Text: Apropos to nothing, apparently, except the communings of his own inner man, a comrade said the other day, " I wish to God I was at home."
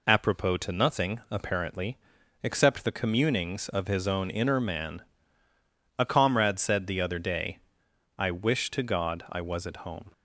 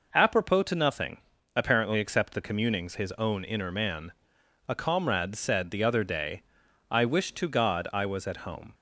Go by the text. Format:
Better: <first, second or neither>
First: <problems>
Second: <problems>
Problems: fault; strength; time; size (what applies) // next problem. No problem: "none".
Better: first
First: none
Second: skips "of"; at 2.9 s